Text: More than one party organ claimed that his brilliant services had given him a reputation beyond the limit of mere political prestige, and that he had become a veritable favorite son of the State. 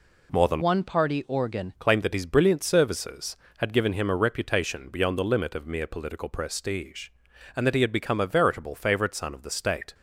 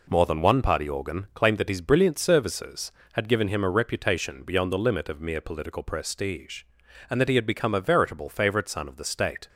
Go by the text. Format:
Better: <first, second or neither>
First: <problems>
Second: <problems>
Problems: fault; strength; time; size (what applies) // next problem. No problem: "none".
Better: second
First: changes voice from "one" to "organ"; from 0.6 to 1.7 s; 1.1 s long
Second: none